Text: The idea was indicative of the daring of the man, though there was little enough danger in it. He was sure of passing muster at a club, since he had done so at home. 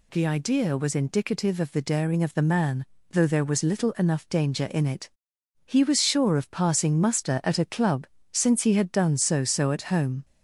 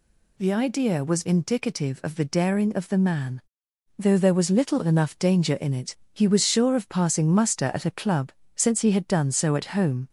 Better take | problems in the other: second | says "so" twice; at 9.4 s

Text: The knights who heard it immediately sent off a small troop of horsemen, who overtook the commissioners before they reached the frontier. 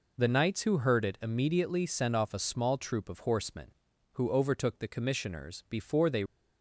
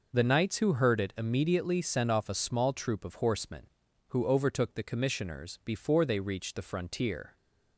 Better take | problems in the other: second | stops before "reached the frontier"; at 6.2 s

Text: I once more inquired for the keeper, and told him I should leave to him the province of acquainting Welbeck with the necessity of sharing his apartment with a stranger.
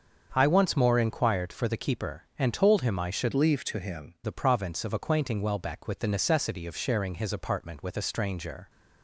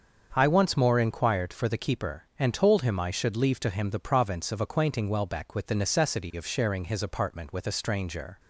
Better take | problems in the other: second | starts louder than the rest; until 1.3 s; 7 dB; also in the second // changes voice from "leave" to "him"; from 3.3 to 4.1 s; 0.8 s long

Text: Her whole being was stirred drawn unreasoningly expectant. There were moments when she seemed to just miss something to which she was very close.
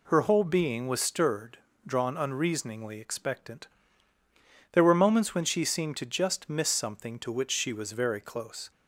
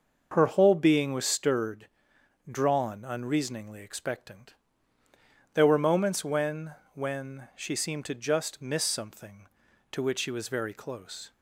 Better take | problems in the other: first | starts louder than the rest; noticeable; until 1.3 s; 6 dB // pauses between "stirred" and "drawn"; noticeable; at 1.8 s; 0.62 s long; slight in the first // says "when" twice; at 6.9 s

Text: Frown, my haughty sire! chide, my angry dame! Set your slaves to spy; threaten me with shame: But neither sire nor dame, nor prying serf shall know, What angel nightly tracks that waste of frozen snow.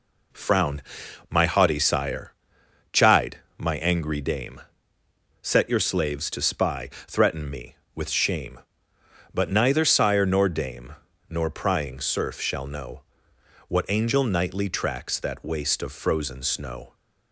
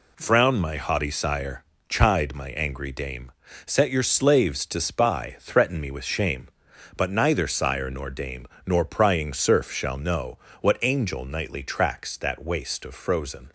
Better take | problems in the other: first | stops before "snow"; at 13.4 s

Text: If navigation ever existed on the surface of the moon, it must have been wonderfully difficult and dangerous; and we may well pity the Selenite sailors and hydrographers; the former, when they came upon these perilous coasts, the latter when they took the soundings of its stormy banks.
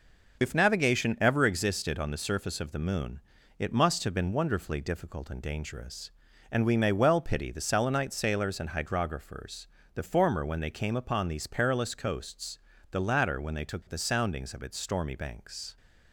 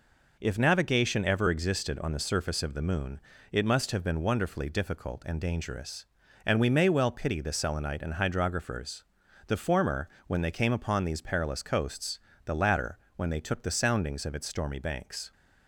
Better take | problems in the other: first | skips "sailors"; at 8.0 s // pauses between "latter" and "when"; slight; at 12.9 s; 0.18 s long

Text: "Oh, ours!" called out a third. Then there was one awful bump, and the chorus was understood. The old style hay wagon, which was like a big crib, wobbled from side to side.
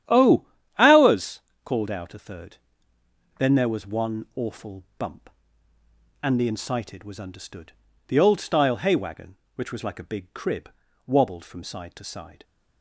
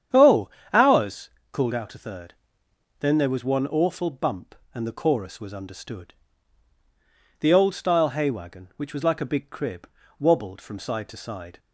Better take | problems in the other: second | starts louder than the rest; strong; until 1.4 s; 10.5 dB; strong in the second // pauses between "awful" and "bump"; slight; at 4.8 s; 0.16 s long // says "incited" for "chorus"; at 6.4 s

